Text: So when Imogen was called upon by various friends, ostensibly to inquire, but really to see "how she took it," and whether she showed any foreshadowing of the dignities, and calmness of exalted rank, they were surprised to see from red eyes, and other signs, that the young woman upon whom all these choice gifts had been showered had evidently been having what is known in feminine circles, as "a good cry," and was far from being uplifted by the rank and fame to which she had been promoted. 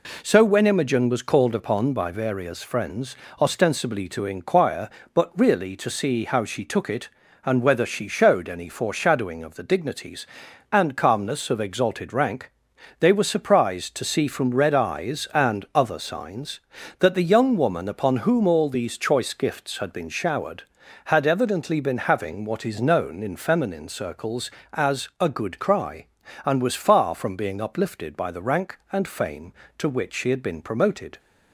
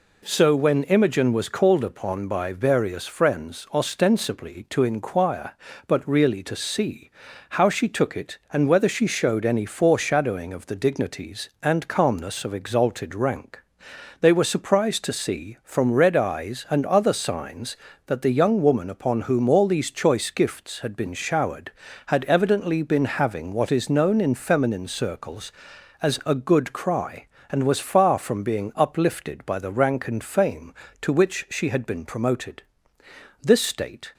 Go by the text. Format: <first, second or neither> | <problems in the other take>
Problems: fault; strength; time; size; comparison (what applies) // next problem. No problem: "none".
first | pauses between "see" and "how"; at 7.0 s; 0.40 s long // goes on to say "This state"; noticeable; from 33.4 s on; 0.70 s long